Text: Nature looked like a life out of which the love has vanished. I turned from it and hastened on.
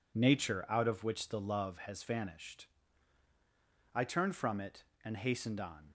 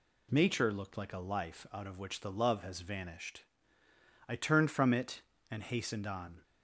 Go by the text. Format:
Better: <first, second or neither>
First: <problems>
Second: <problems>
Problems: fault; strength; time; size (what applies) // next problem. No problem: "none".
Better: second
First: skips "looked like a life"; at 0.6 s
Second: none